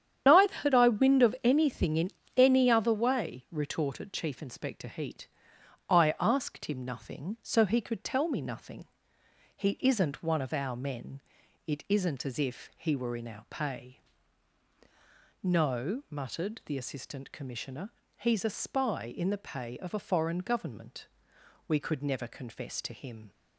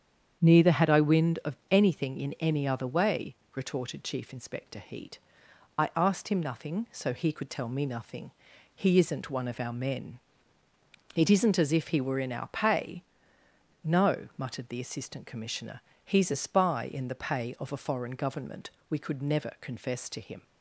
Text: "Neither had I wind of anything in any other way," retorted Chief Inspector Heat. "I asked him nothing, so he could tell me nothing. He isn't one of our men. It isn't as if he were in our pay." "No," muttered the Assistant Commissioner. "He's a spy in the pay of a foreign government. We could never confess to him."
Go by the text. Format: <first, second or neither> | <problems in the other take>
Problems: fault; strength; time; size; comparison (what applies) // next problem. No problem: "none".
second | loses the start of "Neither"; at 0.2 s; 60 ms // starts louder than the rest; strong; until 1.2 s; 9 dB; strong in the second // pauses between "in" and "any"; slight; at 2.1 s; 0.26 s long